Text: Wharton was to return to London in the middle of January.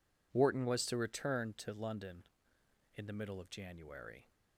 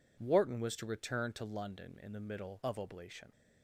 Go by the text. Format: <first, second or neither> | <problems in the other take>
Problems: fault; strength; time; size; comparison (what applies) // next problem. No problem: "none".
first | says "Oblation" for "January"; at 2.7 s